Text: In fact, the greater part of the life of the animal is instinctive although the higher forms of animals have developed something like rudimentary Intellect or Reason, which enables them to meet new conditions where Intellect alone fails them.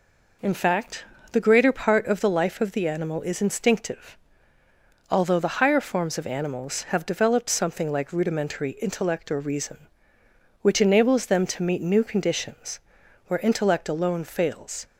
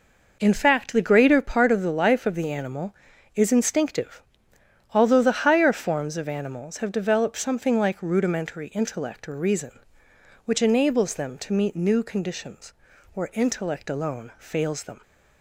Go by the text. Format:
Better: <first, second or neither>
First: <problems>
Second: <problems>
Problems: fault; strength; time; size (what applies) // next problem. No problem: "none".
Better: second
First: pauses between "instinctive" and "although"; noticeable; at 4.1 s; 0.96 s long // pauses between "conditions" and "where"; noticeable; at 12.7 s; 0.48 s long // stops before "them"; at 14.8 s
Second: pauses between "instinctive" and "although"; noticeable; at 4.2 s; 0.72 s long // pauses between "conditions" and "where"; at 12.7 s; 0.42 s long